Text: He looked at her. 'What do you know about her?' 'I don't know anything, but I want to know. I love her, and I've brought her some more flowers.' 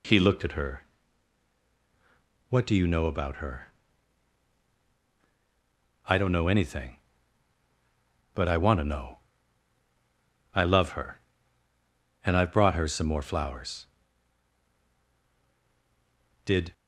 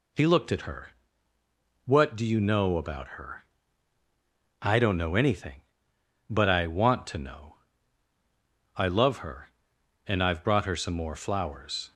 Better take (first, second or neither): second